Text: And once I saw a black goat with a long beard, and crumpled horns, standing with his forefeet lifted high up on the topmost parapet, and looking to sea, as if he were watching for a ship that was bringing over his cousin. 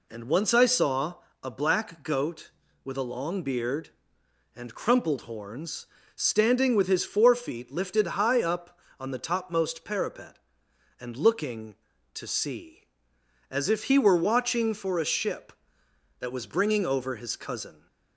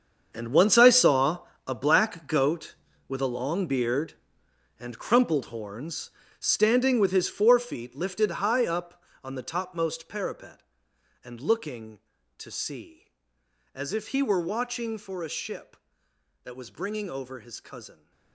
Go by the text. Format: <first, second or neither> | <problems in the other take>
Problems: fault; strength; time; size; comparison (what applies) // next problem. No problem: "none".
first | gets quieter; strong; throughout; 14 dB // pauses between "saw" and "a"; slight; at 1.3 s; 0.28 s long; slight in the first